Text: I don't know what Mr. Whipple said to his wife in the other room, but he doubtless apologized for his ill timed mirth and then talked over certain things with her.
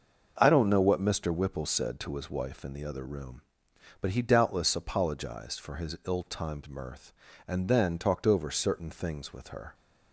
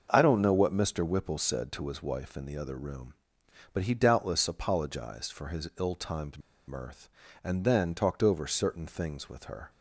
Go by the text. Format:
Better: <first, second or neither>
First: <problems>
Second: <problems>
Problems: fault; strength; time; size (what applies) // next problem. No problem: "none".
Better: first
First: starts louder than the rest; noticeable; until 1.3 s; 6 dB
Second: starts louder than the rest; noticeable; until 1.1 s; 6 dB // pauses between "timed" and "mirth"; slight; at 6.3 s; 0.28 s long